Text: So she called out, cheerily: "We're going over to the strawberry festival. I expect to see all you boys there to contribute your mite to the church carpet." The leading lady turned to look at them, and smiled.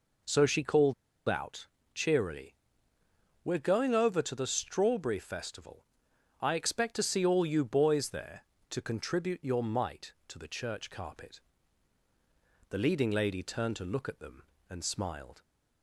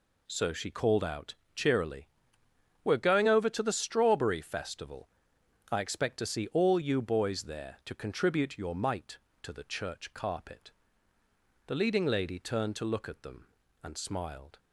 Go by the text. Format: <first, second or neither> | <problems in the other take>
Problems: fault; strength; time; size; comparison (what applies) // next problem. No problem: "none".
second | pauses between "called" and "out"; slight; at 0.9 s; 0.35 s long